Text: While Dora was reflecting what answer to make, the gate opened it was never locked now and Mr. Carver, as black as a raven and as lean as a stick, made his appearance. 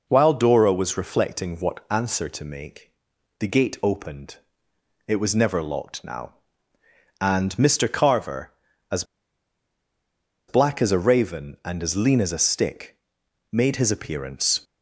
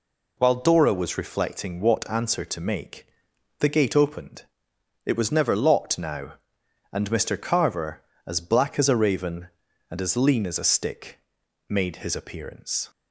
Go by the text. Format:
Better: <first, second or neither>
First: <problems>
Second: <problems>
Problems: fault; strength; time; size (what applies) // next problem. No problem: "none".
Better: second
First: pauses between "opened" and "it"; noticeable; at 4.3 s; 0.68 s long // pauses between "as" and "black"; strong; at 9.0 s; 1.4 s long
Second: pauses between "opened" and "it"; noticeable; at 4.4 s; 0.62 s long